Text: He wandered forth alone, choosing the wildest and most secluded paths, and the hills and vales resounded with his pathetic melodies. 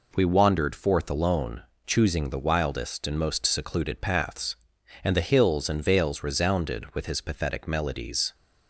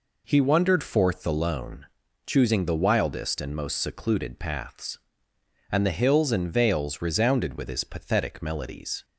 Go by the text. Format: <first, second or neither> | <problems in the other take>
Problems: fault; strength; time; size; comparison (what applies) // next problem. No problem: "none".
second | says "We" for "He"; at 0.1 s